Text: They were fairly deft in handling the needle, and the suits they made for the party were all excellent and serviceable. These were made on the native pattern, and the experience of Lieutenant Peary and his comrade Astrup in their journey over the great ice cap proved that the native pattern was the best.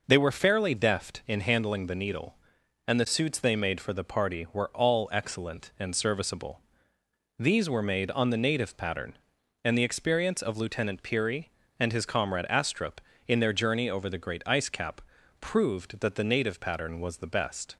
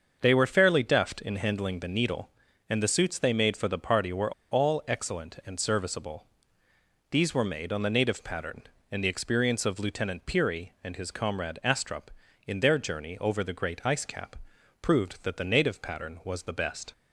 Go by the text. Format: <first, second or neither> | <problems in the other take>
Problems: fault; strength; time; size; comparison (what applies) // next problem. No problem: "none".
first | starts louder than the rest; until 1.2 s; 6.5 dB // pauses between "were" and "all"; slight; at 4.3 s; 0.20 s long // pauses between "cap" and "proved"; noticeable; at 14.3 s; 0.46 s long; also in the first